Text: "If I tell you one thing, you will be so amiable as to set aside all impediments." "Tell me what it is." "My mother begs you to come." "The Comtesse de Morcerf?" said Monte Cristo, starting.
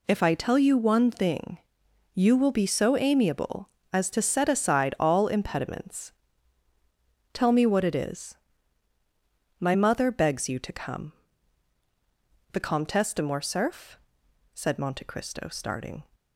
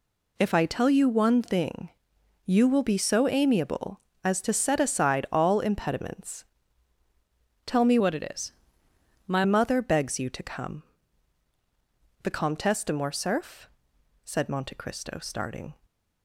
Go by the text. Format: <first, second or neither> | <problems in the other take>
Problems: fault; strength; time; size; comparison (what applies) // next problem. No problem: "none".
first | changes voice from "what" to "My"; from 7.9 to 9.4 s; 1.5 s long // stays silent after the last word; slight; from 15.7 s on; 0.5 s long